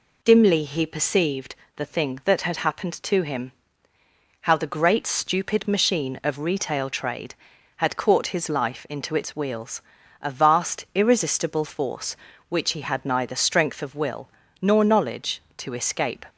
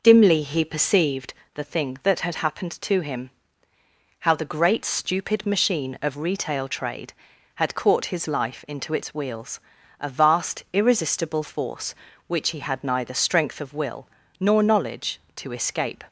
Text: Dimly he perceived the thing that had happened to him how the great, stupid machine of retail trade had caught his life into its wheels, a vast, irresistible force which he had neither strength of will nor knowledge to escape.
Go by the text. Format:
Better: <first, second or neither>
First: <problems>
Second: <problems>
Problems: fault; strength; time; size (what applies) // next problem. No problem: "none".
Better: first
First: pauses between "perceived" and "the"; slight; at 1.5 s; 0.20 s long // pauses between "him" and "how"; noticeable; at 3.5 s; 0.90 s long // pauses between "will" and "nor"; slight; at 14.2 s; 0.32 s long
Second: starts louder than the rest; noticeable; until 1.5 s; 5.5 dB // pauses between "perceived" and "the"; slight; at 1.3 s; 0.20 s long // pauses between "him" and "how"; noticeable; at 3.3 s; 0.90 s long // pauses between "will" and "nor"; slight; at 14.0 s; 0.32 s long